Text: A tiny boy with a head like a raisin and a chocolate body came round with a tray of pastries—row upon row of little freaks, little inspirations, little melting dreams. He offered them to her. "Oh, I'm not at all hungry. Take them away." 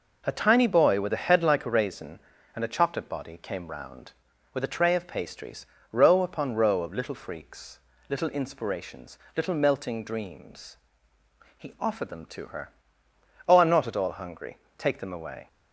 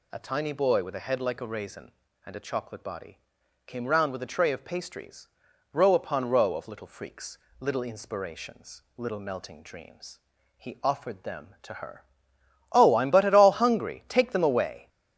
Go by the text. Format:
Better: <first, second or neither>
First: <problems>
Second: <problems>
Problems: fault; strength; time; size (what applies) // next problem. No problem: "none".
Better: first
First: none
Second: pauses between "body" and "came"; noticeable; at 3.2 s; 0.46 s long // says "but" for "not"; at 13.1 s